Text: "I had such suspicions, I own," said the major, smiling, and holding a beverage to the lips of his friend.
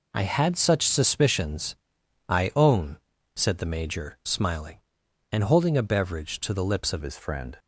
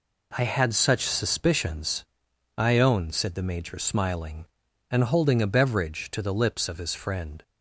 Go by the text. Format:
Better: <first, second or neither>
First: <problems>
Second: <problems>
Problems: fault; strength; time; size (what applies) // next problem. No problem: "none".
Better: second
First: changes voice at "his"; from 7.0 s on; 0.5 s long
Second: none